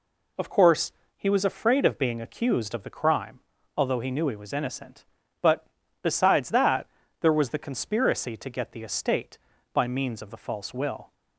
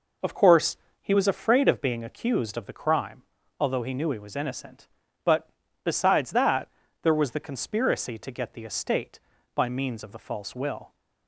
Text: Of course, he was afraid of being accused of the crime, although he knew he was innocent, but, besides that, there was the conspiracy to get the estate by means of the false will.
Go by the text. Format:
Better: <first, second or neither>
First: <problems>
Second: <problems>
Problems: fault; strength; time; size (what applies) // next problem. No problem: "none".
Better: first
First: none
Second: starts louder than the rest; noticeable; until 1.8 s; 5 dB